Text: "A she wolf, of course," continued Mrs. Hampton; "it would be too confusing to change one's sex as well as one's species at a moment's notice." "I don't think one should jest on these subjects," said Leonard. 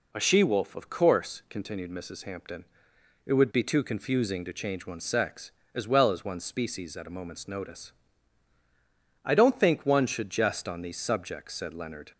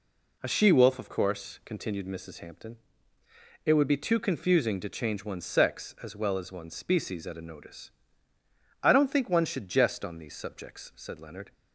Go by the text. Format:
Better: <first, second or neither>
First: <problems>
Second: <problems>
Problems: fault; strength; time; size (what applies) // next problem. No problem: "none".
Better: first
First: none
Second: skips "moment's"; at 7.4 s